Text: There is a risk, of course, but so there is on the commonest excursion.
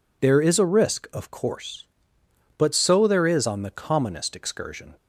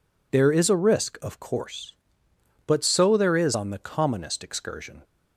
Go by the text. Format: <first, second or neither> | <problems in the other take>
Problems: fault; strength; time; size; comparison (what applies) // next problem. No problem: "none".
neither | none